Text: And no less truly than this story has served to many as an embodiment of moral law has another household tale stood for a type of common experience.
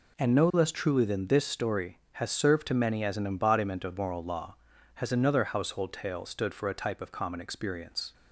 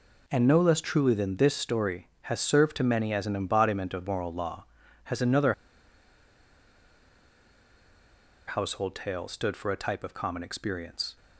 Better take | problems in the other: first | pauses between "another" and "household"; strong; at 5.5 s; 2.9 s long

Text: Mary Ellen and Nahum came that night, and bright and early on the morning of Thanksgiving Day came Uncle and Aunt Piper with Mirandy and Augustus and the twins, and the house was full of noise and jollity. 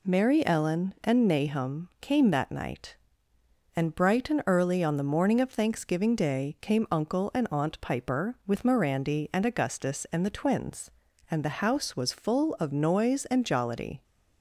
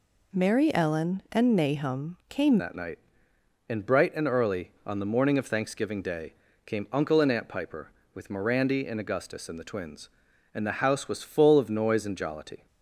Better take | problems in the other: first | changes voice at "that"; from 2.5 s on; 10.1 s long // pauses between "Day" and "came"; slight; at 6.3 s; 0.30 s long

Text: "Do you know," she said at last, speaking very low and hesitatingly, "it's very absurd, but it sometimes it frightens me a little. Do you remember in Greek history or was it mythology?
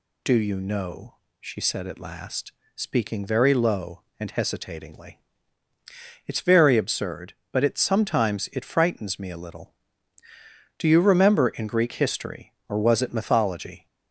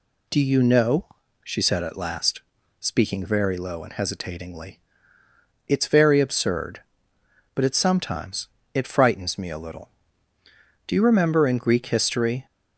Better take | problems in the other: first | pauses between "sometimes" and "it"; slight; at 8.4 s; 0.26 s long // stops before "or was it mythology"; at 12.4 s

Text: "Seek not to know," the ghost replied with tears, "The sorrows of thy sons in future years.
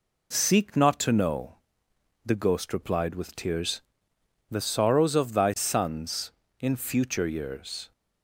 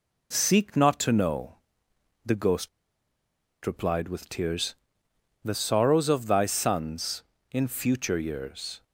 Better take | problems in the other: first | pauses between "ghost" and "replied"; noticeable; at 2.6 s; 0.96 s long

